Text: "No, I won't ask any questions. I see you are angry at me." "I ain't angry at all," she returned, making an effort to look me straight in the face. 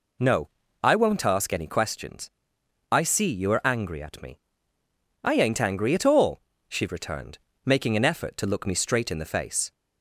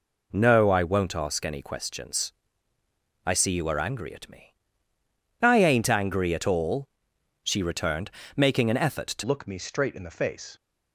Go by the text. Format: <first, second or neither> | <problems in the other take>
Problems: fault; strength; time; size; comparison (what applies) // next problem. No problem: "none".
first | changes voice at "look"; from 9.2 s on; 1.3 s long